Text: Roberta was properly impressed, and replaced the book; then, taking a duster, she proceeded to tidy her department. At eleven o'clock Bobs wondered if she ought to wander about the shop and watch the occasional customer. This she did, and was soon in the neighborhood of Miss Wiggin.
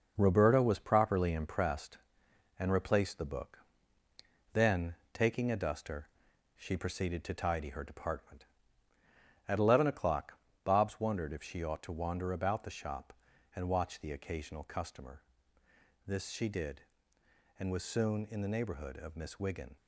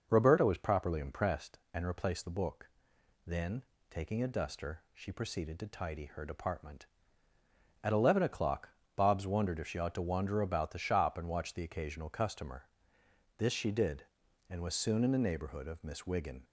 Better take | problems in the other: second | gets quieter; throughout; 6.5 dB // pauses between "o'clock" and "Bobs"; slight; at 10.3 s; 0.26 s long; slight in the second

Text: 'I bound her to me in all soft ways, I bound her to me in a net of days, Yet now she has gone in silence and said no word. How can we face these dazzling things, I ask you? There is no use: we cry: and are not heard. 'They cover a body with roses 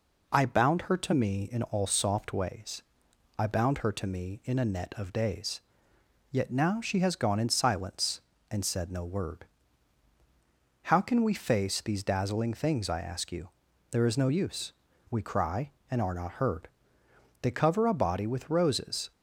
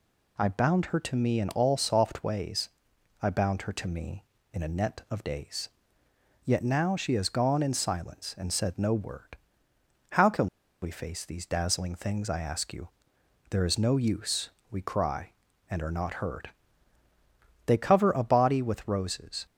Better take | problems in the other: first | pauses between "can" and "we"; at 10.4 s; 0.36 s long

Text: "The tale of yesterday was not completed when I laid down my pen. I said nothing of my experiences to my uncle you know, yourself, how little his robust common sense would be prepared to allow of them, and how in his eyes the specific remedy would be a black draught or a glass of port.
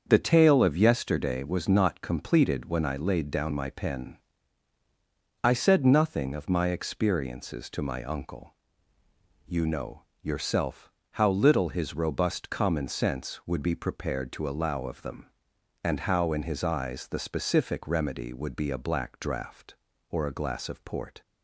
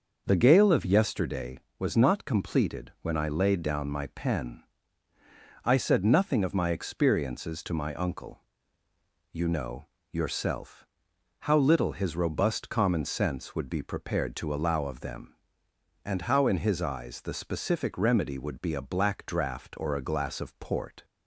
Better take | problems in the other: first | starts louder than the rest; until 1.2 s; 6 dB; also in the first // says "gale" for "tale"; at 0.3 s // pauses between "uncle" and "you"; noticeable; at 8.4 s; 0.92 s long; noticeable in the first

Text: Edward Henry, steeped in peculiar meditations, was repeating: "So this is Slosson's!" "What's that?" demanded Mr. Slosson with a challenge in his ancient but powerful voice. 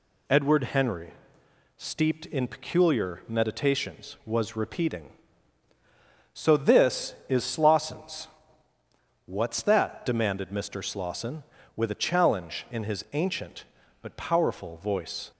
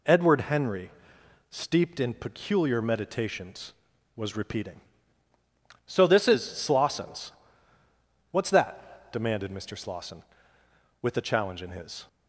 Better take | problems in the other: first | stops before "ancient but powerful voice"; at 12.0 s

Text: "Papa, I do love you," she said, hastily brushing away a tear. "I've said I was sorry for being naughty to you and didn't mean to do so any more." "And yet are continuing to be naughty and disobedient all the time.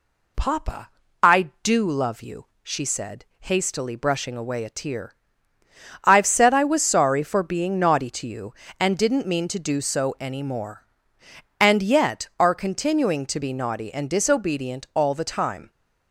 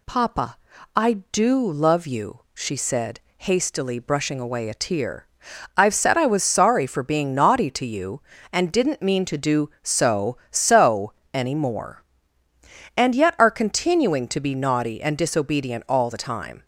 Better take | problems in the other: first | says "so" twice; at 10.5 s

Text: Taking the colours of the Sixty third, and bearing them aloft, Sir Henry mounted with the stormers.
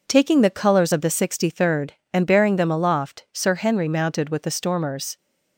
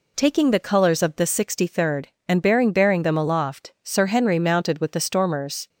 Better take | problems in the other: first | says "bearing" twice; at 2.7 s

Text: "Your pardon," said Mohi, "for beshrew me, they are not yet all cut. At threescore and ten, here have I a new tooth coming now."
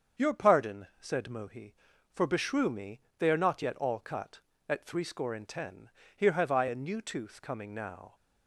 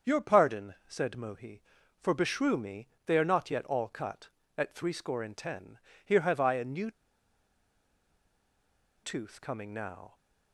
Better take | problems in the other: first | starts louder than the rest; until 1.1 s; 7 dB; also in the first // pauses between "new" and "tooth"; strong; at 6.9 s; 2.1 s long

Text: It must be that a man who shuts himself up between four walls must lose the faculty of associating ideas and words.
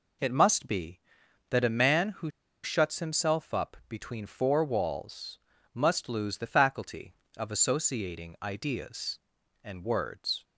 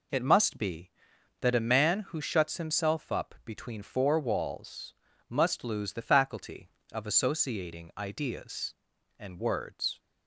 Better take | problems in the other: second | pauses between "who" and "shuts"; slight; at 2.2 s; 0.34 s long // pauses between "walls" and "must"; slight; at 5.3 s; 0.34 s long; slight in the second

